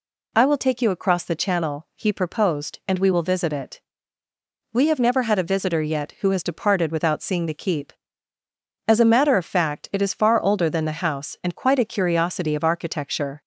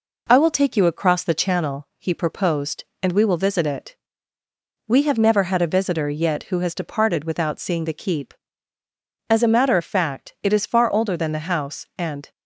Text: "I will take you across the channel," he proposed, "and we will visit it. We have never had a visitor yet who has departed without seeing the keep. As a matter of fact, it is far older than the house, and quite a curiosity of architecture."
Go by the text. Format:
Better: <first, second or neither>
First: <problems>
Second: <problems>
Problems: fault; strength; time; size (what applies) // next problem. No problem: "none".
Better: first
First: none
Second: stops before "quite a curiosity of architecture"; at 12.3 s